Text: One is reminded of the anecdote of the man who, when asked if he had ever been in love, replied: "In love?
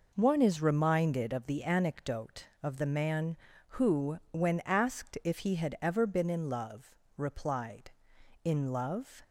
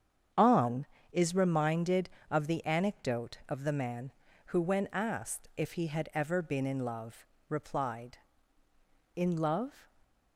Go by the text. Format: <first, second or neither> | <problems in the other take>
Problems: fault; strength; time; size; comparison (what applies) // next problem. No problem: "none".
first | starts louder than the rest; strong; until 1.5 s; 8 dB // says "On" for "One"; at 0.3 s